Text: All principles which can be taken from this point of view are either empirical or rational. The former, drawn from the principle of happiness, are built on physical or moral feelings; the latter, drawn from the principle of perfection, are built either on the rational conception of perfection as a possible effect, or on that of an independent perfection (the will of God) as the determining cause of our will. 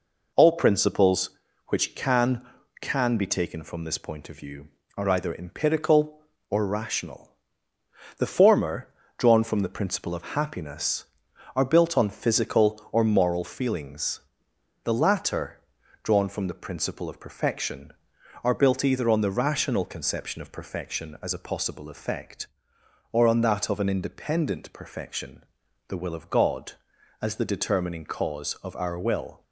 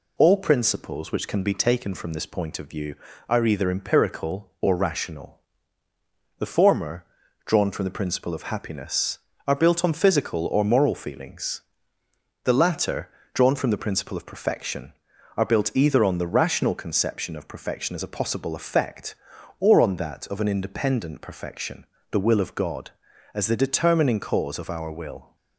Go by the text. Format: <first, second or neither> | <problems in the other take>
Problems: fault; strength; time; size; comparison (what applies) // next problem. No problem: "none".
second | says "can" twice; at 2.8 s